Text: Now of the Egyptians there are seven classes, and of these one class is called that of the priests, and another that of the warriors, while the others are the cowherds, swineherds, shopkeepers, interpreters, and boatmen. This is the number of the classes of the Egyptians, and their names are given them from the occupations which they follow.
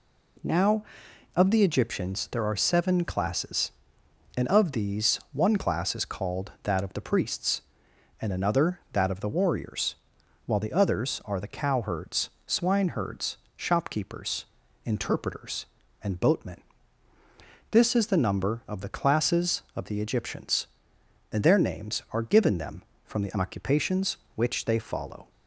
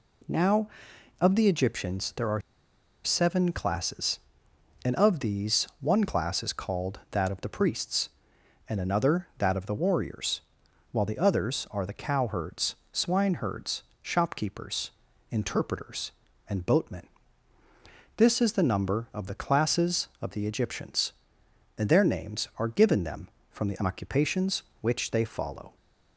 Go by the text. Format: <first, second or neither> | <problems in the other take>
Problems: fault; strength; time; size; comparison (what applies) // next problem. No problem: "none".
first | pauses between "are" and "seven"; noticeable; at 2.4 s; 0.63 s long